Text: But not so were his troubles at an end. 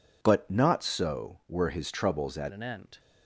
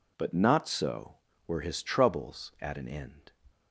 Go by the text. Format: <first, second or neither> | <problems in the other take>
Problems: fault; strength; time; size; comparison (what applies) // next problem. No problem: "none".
second | changes voice at "an"; from 2.5 s on; 0.4 s long